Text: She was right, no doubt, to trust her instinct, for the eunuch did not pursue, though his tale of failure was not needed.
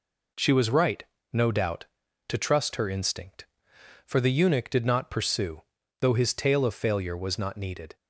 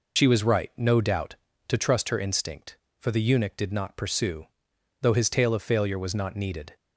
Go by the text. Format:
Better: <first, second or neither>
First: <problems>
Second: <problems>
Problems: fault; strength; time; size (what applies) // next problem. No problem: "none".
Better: first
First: none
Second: loses the start of "She"; at 0.1 s; 60 ms